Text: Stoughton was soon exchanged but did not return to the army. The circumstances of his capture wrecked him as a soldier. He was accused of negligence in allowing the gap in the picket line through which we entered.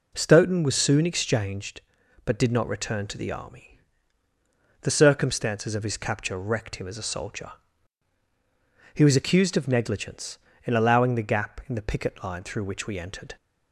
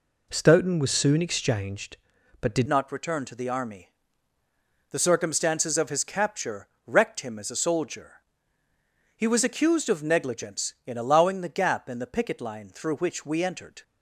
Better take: first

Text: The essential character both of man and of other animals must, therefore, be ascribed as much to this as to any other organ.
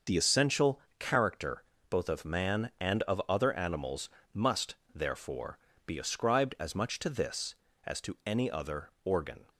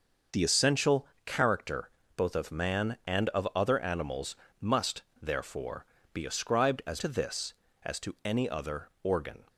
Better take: first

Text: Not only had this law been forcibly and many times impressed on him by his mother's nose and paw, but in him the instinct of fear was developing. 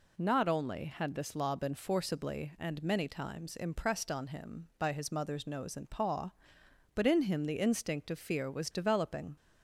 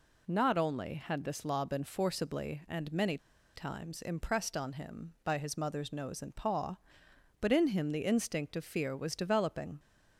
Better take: first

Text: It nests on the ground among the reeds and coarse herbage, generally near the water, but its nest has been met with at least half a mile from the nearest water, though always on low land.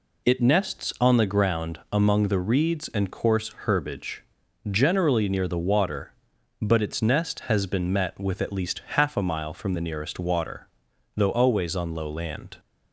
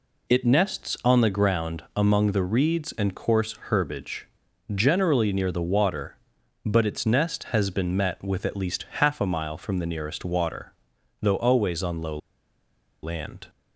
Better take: first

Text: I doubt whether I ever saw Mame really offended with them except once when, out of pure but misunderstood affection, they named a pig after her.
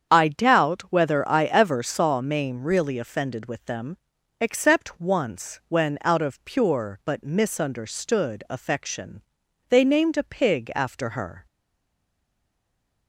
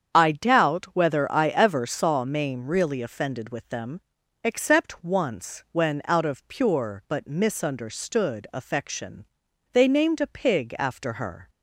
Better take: second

